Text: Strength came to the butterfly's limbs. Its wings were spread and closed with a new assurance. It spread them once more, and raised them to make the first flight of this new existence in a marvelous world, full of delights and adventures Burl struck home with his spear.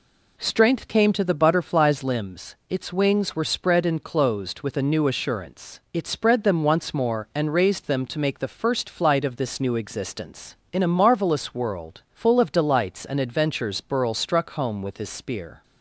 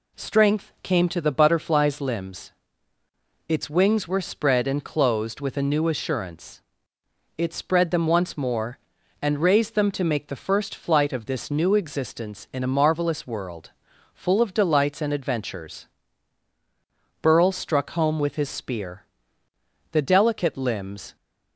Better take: first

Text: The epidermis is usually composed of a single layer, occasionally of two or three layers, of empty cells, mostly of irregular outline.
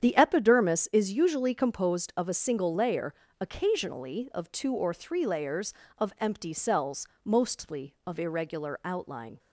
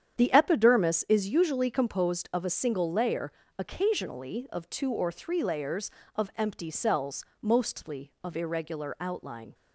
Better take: neither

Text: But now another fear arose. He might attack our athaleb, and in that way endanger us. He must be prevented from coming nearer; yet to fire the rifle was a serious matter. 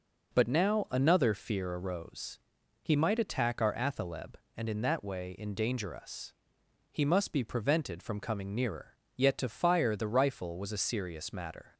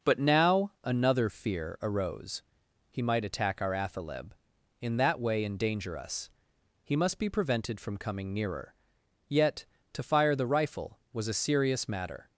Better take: first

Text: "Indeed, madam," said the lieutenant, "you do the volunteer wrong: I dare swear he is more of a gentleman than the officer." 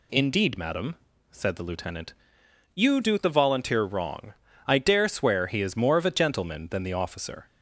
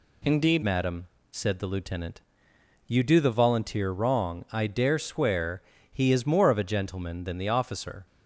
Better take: first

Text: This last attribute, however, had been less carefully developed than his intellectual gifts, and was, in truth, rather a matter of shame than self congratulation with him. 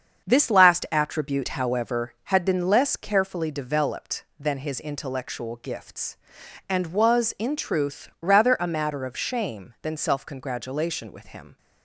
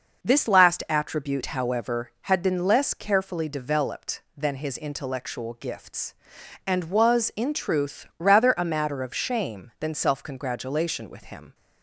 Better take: second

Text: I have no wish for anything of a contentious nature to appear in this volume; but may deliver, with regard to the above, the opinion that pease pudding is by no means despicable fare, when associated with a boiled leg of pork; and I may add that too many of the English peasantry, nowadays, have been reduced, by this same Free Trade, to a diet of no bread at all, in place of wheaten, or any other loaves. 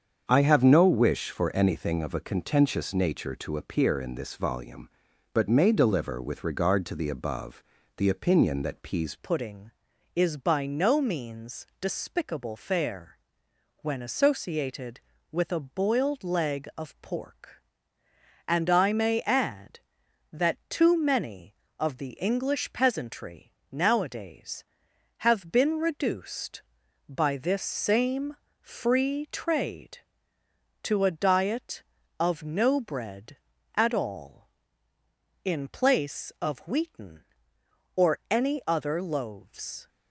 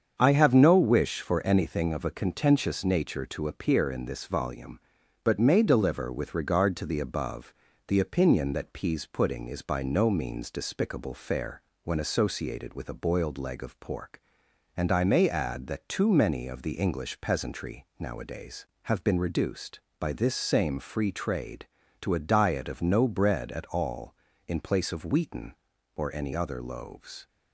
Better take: second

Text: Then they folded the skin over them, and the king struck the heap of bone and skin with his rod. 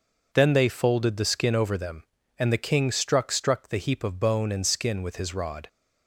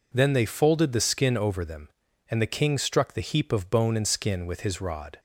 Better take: second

